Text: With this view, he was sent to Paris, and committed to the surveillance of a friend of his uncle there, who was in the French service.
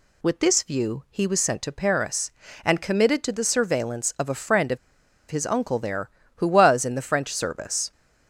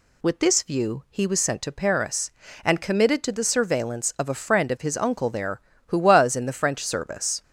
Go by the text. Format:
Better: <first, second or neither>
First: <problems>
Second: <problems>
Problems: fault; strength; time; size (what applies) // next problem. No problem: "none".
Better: second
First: pauses between "of" and "his"; noticeable; at 4.7 s; 0.53 s long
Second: none